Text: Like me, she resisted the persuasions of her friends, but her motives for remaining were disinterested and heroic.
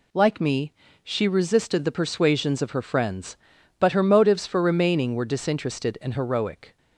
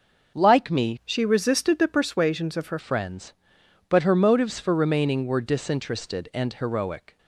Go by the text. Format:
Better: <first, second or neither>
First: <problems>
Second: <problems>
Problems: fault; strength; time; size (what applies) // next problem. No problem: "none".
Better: first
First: none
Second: starts louder than the rest; noticeable; until 1.4 s; 6 dB // changes voice from "she" to "her"; from 1.0 to 2.7 s; 1.7 s long